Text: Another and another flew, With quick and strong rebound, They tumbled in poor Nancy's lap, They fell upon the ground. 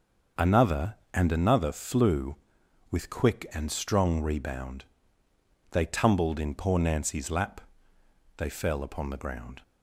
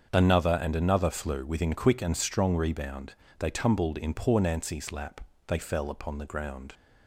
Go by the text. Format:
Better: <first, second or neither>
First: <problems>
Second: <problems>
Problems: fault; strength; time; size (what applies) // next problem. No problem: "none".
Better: first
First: starts louder than the rest; until 1.5 s; 6.5 dB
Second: starts louder than the rest; until 1.1 s; 7 dB // says "Within" for "With"; at 1.4 s